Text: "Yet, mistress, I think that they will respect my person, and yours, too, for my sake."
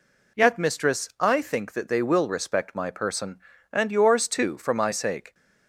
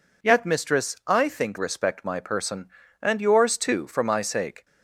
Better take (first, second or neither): first